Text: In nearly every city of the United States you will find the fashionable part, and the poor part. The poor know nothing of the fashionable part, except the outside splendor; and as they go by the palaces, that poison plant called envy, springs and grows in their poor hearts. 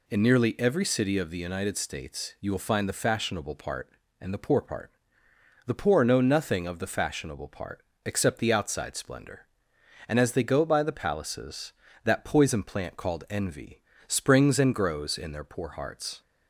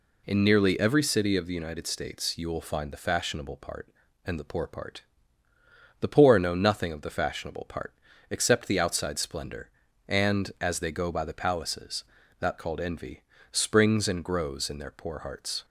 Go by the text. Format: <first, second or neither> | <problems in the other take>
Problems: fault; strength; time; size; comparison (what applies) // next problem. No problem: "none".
first | skips "poison plant"; at 12.5 s